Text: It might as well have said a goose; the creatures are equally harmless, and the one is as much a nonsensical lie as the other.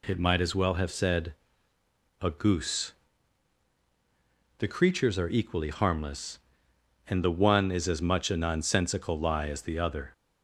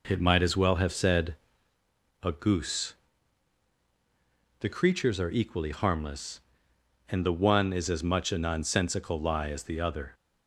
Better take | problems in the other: first | starts louder than the rest; noticeable; until 1.7 s; 4 dB // pauses between "said" and "a"; noticeable; at 1.3 s; 0.88 s long; noticeable in the first

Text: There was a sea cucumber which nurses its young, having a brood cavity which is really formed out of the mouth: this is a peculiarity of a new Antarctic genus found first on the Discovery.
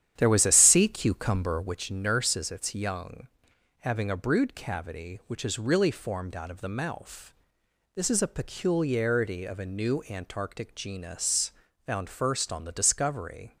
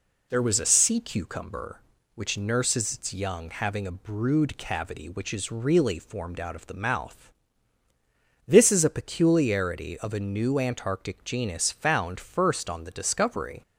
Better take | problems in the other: second | starts louder than the rest; strong; until 1.8 s; 10 dB // pauses between "genus" and "found"; slight; at 11.5 s; 0.34 s long

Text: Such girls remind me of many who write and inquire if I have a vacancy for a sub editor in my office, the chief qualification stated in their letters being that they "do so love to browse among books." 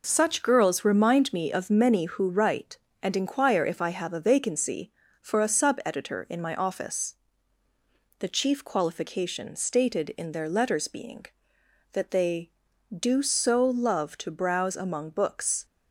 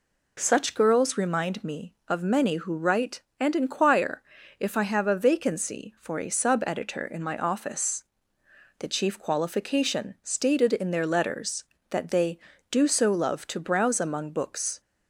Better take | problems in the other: first | pauses between "inquire" and "if"; at 4.2 s; 0.38 s long // skips "being"; at 11.7 s

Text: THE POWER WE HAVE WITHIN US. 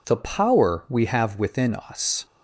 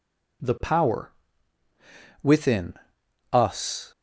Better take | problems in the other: first | skips "WE HAVE"; at 1.6 s // pauses between "WITHIN" and "US"; noticeable; at 2.7 s; 0.58 s long

